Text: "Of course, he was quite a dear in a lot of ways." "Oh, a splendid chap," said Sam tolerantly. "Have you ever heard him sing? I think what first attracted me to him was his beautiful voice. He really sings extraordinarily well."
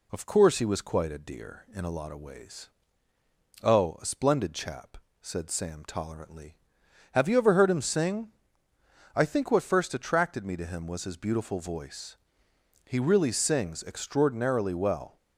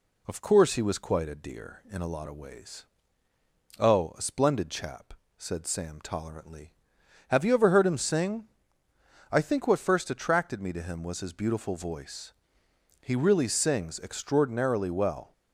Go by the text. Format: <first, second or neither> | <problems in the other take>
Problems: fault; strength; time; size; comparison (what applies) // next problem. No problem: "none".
neither | none